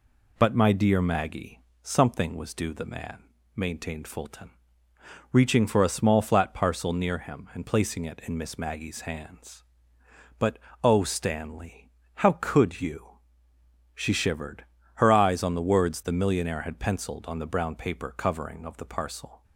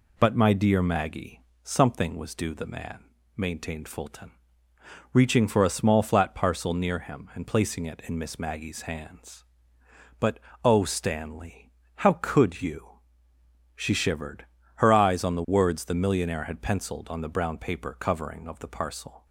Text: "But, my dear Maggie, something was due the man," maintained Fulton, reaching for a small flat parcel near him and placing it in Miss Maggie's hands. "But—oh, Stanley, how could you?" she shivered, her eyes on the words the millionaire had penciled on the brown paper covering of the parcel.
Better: neither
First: none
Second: none

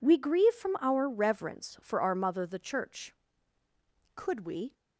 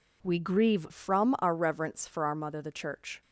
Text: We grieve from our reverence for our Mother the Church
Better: second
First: goes on to say "Could we"; from 4.1 s on; 0.58 s long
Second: none

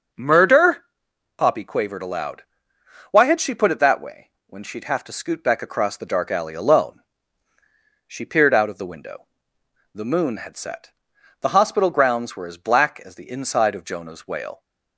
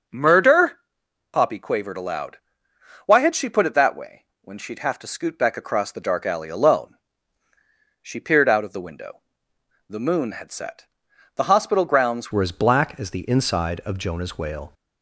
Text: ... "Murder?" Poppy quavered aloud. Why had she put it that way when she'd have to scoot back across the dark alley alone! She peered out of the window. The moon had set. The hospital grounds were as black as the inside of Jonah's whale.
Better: first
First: starts louder than the rest; until 1.6 s; 6 dB // pauses between "way" and "when"; slight; at 4.2 s; 0.16 s long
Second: starts louder than the rest; until 1.6 s; 6 dB // pauses between "way" and "when"; slight; at 4.2 s; 0.16 s long // changes voice at "were"; from 12.3 s on; 2.4 s long

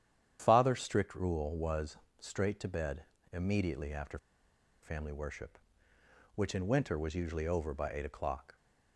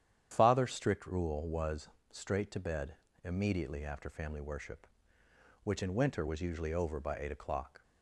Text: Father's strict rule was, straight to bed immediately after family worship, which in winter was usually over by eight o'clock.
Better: second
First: starts louder than the rest; strong; until 1.4 s; 9.5 dB // pauses between "bed" and "immediately"; slight; at 3.0 s; 0.28 s long // pauses between "after" and "family"; noticeable; at 4.1 s; 0.66 s long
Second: starts louder than the rest; strong; until 1.3 s; 9.5 dB // pauses between "bed" and "immediately"; slight; at 2.9 s; 0.28 s long

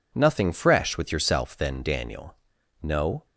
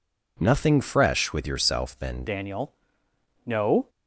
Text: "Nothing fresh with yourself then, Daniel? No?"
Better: first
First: none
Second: changes voice at "Daniel"; from 2.2 s on; 1.6 s long

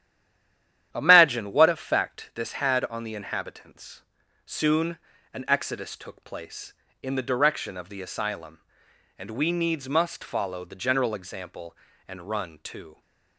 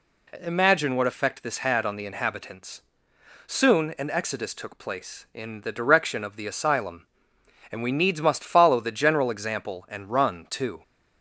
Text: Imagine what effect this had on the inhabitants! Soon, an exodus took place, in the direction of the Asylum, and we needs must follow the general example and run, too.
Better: second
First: stays silent before the first word; slight; until 0.9 s; 0.9 s long // starts louder than the rest; strong; until 1.9 s; 10.5 dB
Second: none

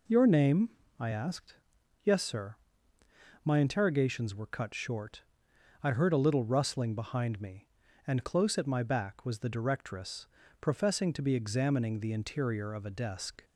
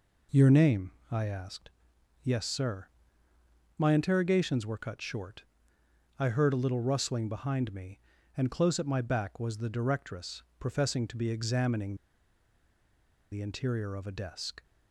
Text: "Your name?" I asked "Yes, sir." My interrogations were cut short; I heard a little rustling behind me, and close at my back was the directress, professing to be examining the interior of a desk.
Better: first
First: pauses between "asked" and "Yes"; noticeable; at 1.5 s; 0.46 s long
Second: pauses between "asked" and "Yes"; noticeable; at 1.6 s; 0.52 s long // pauses between "examining" and "the"; strong; at 11.9 s; 1.3 s long

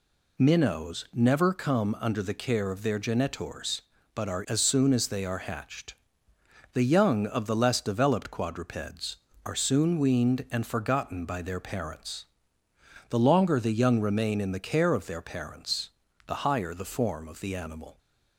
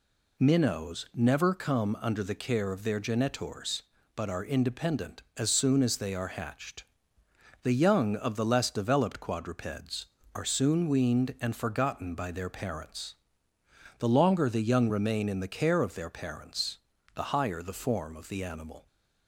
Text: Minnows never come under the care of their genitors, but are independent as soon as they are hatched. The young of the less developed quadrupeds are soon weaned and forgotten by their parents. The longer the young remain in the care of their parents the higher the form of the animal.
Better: second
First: skips "independent"; at 4.4 s // pauses between "parents" and "the"; slight; at 15.8 s; 0.36 s long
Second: pauses between "parents" and "the"; slight; at 16.7 s; 0.36 s long

